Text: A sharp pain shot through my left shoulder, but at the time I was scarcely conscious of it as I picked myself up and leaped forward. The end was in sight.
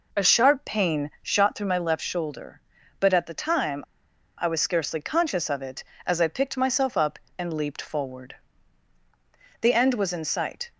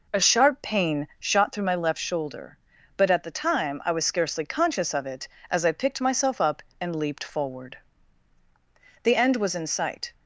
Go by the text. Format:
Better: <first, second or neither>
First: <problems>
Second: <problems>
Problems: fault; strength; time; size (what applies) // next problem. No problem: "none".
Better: second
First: pauses between "time" and "I"; noticeable; at 3.8 s; 0.54 s long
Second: none